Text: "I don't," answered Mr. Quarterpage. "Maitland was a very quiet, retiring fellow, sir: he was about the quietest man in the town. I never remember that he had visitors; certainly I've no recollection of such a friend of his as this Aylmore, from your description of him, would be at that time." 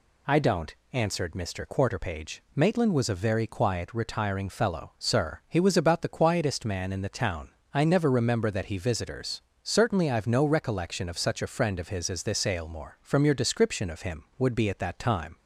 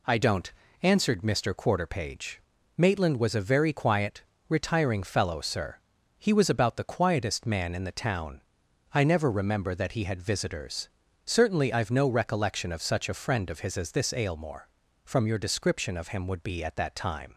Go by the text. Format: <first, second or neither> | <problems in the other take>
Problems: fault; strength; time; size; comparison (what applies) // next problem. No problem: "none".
second | skips "had"; at 8.7 s